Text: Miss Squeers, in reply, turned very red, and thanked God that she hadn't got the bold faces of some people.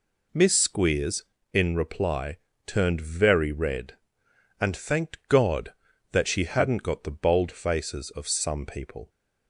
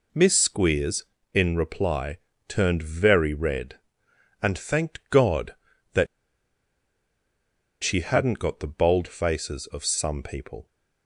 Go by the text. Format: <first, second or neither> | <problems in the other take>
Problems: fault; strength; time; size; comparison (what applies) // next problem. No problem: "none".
first | pauses between "that" and "she"; strong; at 6.0 s; 1.7 s long